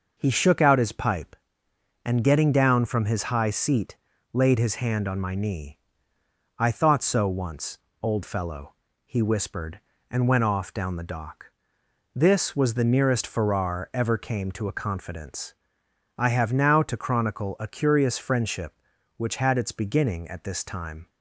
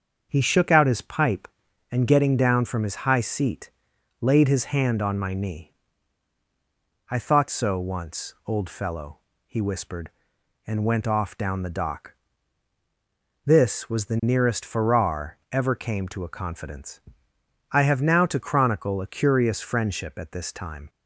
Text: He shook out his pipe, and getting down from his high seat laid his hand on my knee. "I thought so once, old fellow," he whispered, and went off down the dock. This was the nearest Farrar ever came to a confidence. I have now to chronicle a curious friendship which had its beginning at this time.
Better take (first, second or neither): first